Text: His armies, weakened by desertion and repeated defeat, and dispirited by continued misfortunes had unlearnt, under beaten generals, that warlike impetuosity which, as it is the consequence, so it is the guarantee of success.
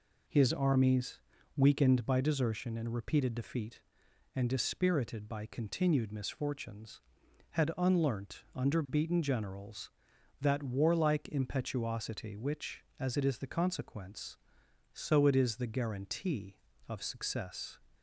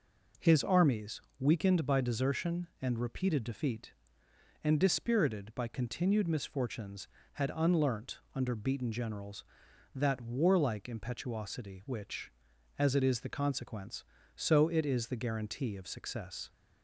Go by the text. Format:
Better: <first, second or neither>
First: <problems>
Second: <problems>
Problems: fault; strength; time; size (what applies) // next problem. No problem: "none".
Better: neither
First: none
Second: none